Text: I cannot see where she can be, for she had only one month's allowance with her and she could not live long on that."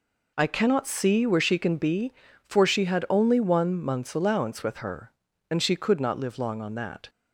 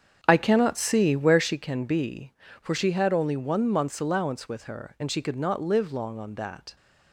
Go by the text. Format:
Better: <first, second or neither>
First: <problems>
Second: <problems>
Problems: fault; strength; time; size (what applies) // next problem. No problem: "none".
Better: first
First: none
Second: starts louder than the rest; strong; until 1.5 s; 8 dB